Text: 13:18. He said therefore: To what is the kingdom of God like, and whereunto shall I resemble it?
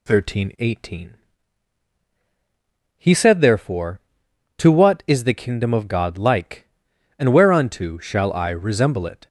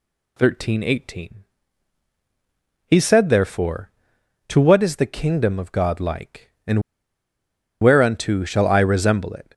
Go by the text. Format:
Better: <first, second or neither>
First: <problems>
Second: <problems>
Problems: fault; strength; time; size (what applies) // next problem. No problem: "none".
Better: first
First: none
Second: pauses between "and" and "whereunto"; at 6.8 s; 1.0 s long